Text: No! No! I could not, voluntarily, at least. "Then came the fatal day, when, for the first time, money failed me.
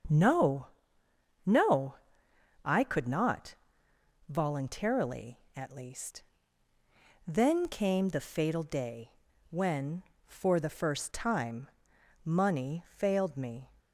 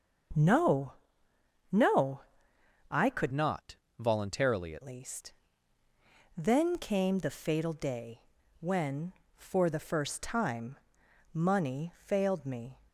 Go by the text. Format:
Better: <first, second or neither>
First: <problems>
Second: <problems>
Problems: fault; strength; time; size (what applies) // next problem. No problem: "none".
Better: first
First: starts louder than the rest; until 1.8 s; 7 dB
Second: starts louder than the rest; until 2.1 s; 6.5 dB // changes voice from "not" to "at"; from 3.3 to 4.8 s; 1.5 s long